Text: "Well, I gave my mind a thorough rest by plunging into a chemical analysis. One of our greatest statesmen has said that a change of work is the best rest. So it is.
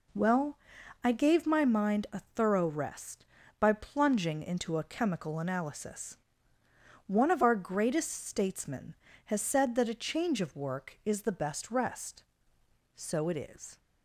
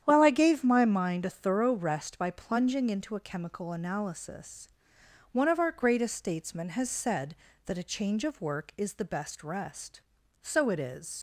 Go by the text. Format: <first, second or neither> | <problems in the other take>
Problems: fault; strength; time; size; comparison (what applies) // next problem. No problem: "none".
first | starts louder than the rest; strong; until 1.0 s; 9.5 dB // leaves "is" unfinished; at 11.1 s; 65 ms